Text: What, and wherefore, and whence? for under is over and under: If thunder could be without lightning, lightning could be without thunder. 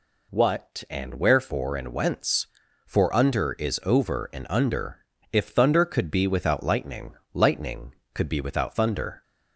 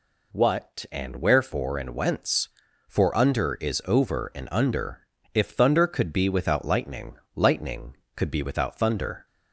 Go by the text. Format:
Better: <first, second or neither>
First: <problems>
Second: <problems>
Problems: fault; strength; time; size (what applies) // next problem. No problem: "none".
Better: neither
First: none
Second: none